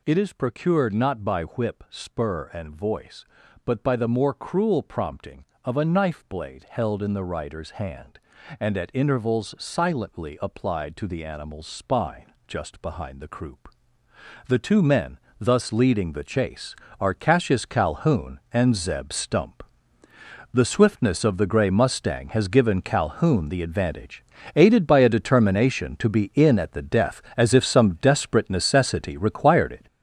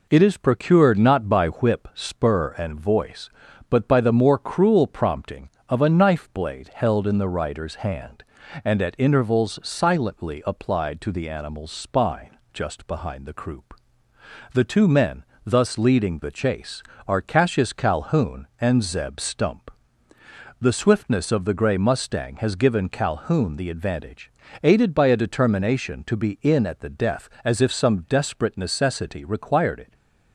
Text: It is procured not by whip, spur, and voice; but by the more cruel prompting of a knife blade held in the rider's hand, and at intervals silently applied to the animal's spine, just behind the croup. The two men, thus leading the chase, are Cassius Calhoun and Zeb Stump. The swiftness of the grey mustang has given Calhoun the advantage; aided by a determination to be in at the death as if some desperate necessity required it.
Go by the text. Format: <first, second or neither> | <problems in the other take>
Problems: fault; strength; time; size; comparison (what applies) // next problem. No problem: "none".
second | gets louder; strong; throughout; 8.5 dB